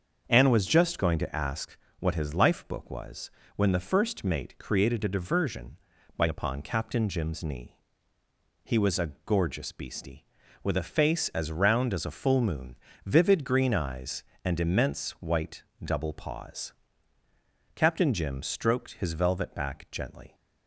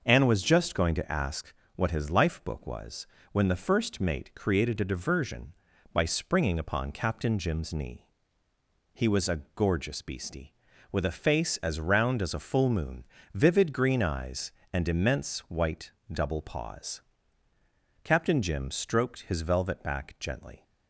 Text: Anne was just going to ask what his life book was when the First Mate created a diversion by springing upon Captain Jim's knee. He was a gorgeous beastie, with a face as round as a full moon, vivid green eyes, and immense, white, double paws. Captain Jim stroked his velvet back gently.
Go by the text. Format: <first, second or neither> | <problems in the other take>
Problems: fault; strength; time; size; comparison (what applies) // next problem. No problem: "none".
second | starts louder than the rest; until 1.2 s; 7 dB; noticeable in the second // pauses between "ask" and "what"; slight; at 1.7 s; 0.22 s long; slight in the second // pauses between "was" and "when"; slight; at 3.3 s; 0.26 s long; slight in the second // skips "springing"; at 6.2 s